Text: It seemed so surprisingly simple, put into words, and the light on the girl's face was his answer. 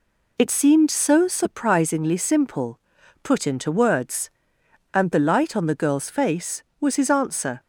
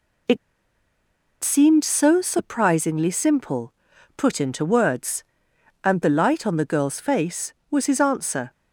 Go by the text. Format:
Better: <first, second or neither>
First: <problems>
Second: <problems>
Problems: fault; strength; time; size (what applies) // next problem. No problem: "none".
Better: first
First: none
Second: pauses between "It" and "seemed"; at 0.3 s; 1.0 s long